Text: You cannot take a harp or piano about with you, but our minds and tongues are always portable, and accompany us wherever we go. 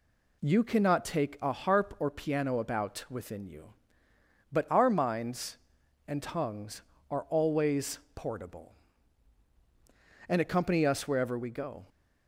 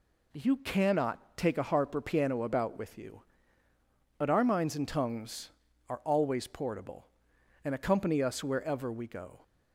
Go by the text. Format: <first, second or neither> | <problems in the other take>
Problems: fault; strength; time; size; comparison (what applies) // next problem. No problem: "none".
second | says "within" for "with"; at 3.0 s // pauses between "always" and "portable"; slight; at 7.9 s; 0.16 s long